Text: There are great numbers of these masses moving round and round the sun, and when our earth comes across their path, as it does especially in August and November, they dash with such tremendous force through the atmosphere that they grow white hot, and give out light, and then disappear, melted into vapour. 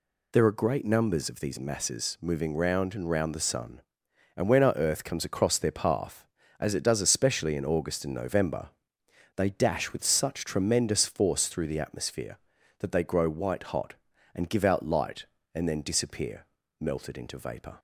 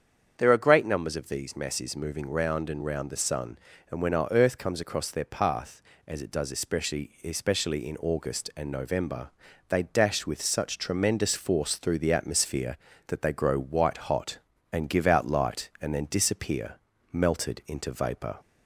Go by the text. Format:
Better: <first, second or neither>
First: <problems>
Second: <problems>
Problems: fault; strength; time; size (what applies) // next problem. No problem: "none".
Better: first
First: none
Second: starts louder than the rest; strong; until 1.3 s; 7.5 dB // says "especially" twice; at 7.2 s